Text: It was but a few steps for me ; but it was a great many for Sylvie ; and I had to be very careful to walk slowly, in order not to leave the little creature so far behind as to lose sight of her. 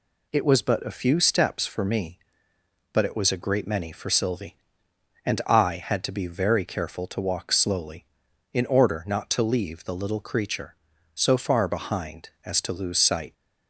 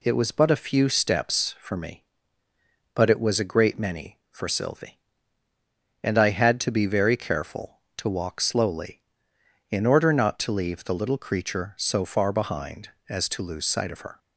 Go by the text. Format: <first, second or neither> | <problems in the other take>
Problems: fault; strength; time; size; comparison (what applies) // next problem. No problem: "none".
second | stops before "of her"; at 13.3 s